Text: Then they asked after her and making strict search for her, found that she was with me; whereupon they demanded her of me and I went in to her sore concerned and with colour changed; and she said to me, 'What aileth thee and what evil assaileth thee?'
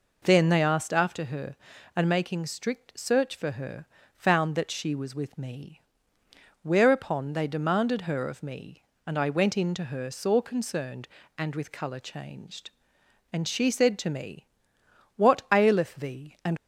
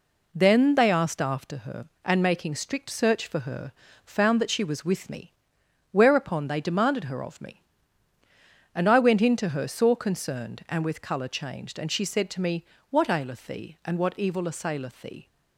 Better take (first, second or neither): second